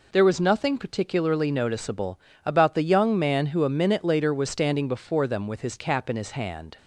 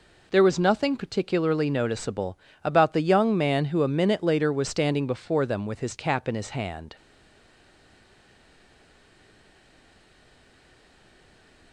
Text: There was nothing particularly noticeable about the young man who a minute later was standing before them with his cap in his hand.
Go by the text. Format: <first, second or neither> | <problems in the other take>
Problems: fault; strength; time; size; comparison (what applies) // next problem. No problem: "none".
first | pauses between "noticeable" and "about"; slight; at 2.3 s; 0.28 s long; slight in the first // stays silent after the last word; strong; from 6.9 s on; 4.8 s long